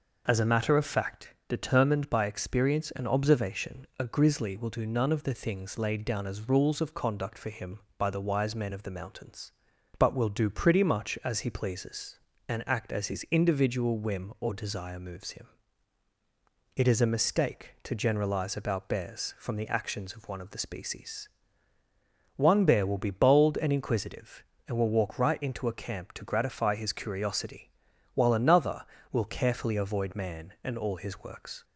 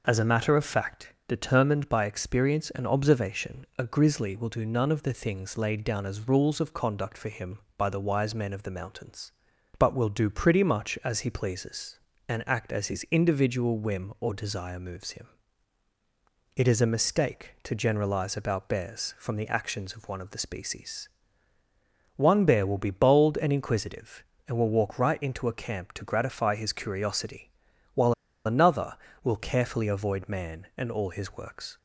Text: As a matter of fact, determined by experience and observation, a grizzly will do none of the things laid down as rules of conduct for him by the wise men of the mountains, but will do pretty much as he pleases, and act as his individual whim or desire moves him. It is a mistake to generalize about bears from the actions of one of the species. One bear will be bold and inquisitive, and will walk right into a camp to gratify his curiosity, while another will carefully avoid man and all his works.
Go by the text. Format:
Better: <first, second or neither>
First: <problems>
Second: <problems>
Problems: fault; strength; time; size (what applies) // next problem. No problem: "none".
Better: first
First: none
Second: pauses between "while" and "another"; slight; at 28.1 s; 0.33 s long